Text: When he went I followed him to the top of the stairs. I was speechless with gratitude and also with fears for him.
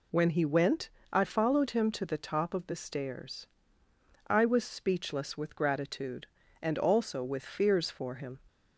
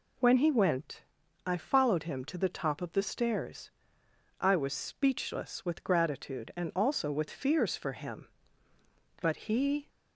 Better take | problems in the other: first | pauses between "went" and "I"; at 1.0 s; 0.42 s long; slight in the first // goes on to say "But he"; noticeable; from 9.2 s on; 0.68 s long

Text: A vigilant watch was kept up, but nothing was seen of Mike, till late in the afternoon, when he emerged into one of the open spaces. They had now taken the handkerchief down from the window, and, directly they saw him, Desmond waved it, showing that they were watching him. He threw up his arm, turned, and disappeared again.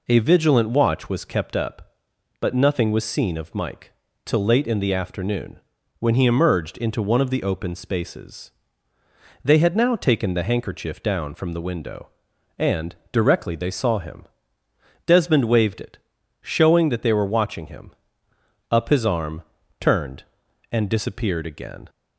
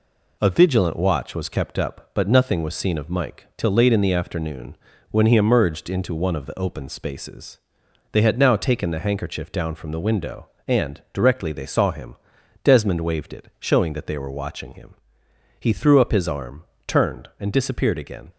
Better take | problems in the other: second | skips "He threw"; at 18.3 s

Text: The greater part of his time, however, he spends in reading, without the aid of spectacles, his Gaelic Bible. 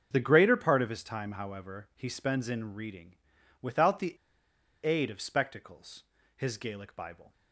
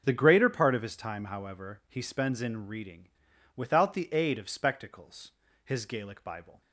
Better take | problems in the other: second | starts louder than the rest; until 1.1 s; 6.5 dB; also in the second // pauses between "the" and "aid"; noticeable; at 4.1 s; 0.70 s long

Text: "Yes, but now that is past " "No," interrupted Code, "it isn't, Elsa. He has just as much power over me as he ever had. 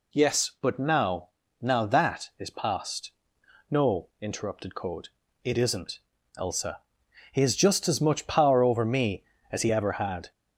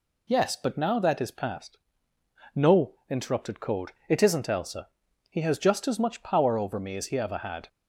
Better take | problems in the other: second | says "now" twice; at 1.6 s

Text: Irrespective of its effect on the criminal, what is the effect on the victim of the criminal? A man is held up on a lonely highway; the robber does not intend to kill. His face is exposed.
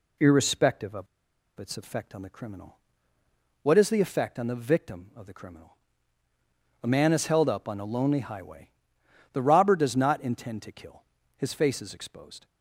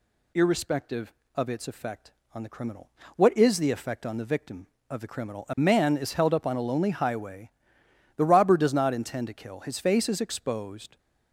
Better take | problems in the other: second | pauses between "of" and "its"; noticeable; at 1.0 s; 0.52 s long

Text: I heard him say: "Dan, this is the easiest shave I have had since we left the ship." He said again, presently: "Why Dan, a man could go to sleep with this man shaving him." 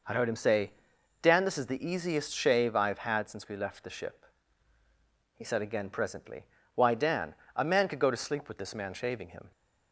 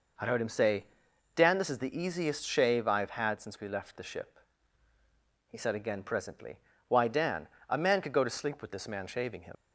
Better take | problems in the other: first | leaves "him" unfinished; at 9.5 s; 90 ms

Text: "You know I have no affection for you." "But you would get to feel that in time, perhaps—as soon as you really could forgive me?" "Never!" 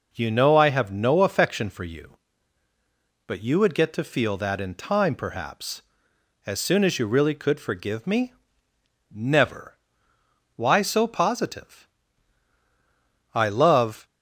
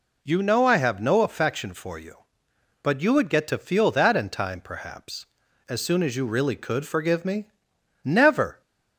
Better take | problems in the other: second | goes on to say "Why so positive I love"; strong; from 10.5 s on; 3.4 s long

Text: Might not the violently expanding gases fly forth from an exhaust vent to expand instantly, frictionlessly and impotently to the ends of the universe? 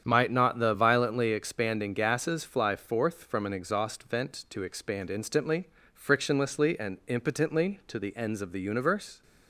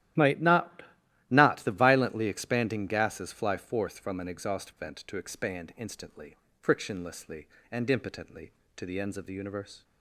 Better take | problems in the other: first | starts louder than the rest; strong; until 1.6 s; 13 dB; strong in the first // says "not" twice; at 1.2 s

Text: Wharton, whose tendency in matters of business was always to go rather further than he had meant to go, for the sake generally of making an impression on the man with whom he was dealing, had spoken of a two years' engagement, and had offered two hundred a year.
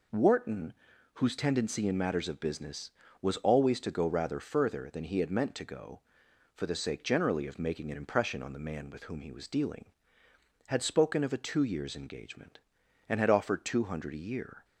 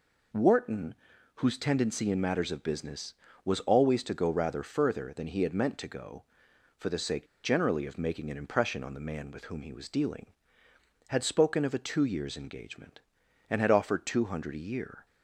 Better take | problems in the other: first | pauses between "sake" and "generally"; slight; at 7.2 s; 0.18 s long

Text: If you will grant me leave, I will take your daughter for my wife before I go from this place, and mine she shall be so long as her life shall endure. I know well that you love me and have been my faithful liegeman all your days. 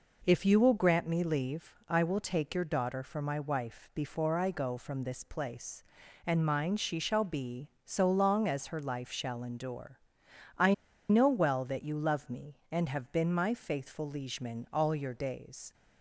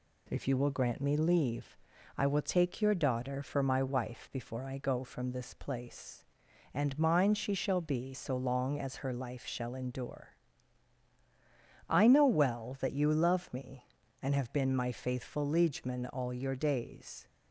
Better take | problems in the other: second | pauses between "I" and "know"; slight; at 10.7 s; 0.35 s long

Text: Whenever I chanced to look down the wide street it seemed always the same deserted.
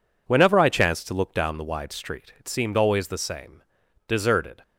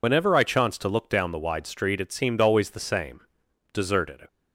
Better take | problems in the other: first | loses the start of "Whenever"; at 0.0 s; 65 ms // pauses between "same" and "deserted"; noticeable; at 3.2 s; 0.52 s long; noticeable in the first

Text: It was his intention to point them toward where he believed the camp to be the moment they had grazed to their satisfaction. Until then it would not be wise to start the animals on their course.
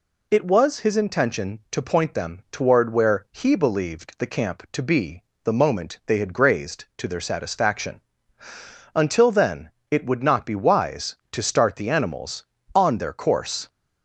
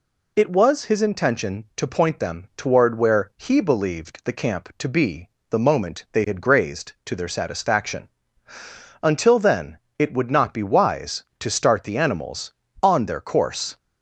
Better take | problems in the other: neither | pauses between "be" and "the"; slight; the same in both // pauses between "then" and "it"; slight; the same in both

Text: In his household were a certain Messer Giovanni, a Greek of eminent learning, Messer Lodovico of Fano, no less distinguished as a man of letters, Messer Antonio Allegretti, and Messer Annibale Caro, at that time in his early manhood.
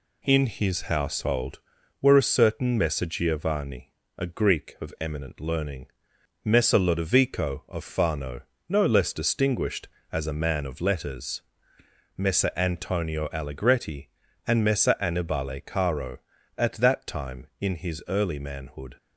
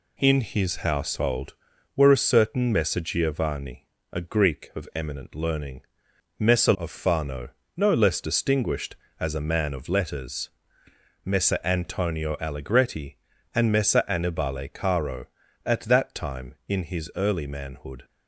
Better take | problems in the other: first | skips "Lodovico"; at 6.7 s

